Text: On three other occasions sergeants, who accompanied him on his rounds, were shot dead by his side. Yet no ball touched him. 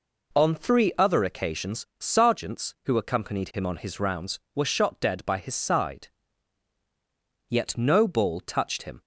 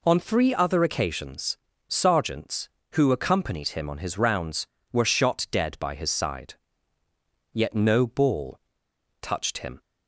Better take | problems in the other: first | pauses between "occasions" and "sergeants"; slight; at 1.5 s; 0.30 s long // pauses between "ball" and "touched"; noticeable; at 8.5 s; 0.63 s long

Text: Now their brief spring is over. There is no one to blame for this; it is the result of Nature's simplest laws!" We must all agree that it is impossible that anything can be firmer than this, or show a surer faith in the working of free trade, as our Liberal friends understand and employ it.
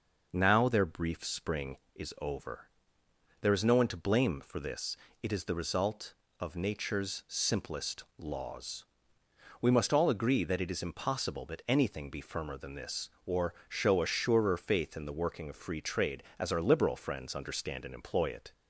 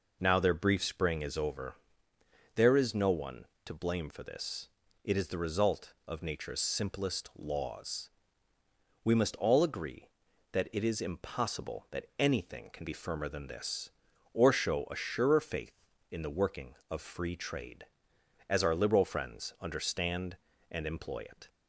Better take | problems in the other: second | skips "can"; at 12.0 s // pauses between "or" and "show"; slight; at 13.5 s; 0.16 s long

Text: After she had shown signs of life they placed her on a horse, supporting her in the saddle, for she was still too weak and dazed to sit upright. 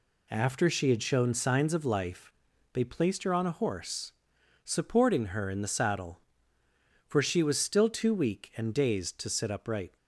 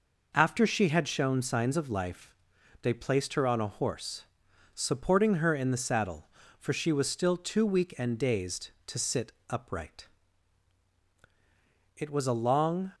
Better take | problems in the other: first | pauses between "life" and "they"; noticeable; at 2.3 s; 0.48 s long; also in the first // pauses between "sit" and "upright"; slight; at 9.3 s; 0.18 s long // goes on to say "It was a long"; noticeable; from 11.9 s on; 0.94 s long

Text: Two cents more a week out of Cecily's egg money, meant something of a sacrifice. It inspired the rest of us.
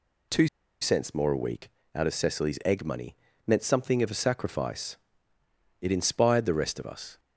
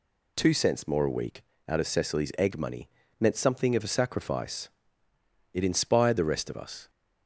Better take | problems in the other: second | pauses between "Two" and "cents"; slight; at 0.4 s; 0.33 s long // pauses between "week" and "out"; slight; at 1.6 s; 0.26 s long; slight in the second

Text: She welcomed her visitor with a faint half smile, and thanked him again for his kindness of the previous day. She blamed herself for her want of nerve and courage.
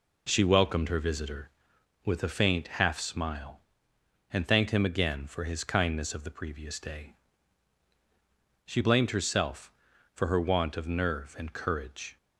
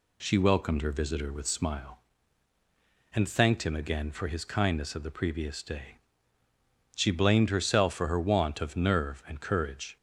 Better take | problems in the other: first | skips "a faint half"; at 1.4 s

